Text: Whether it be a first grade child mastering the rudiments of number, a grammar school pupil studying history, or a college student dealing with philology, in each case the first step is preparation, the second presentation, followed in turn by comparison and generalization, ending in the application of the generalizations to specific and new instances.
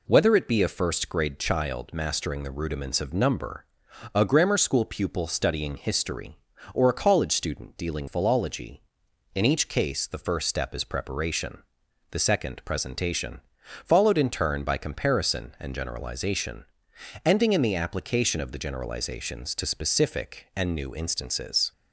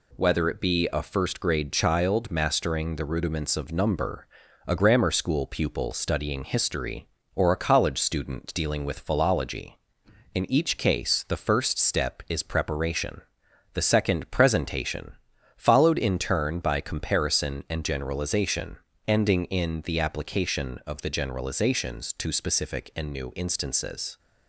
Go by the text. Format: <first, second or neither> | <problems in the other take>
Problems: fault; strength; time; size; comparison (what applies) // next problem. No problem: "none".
second | skips "with"; at 8.0 s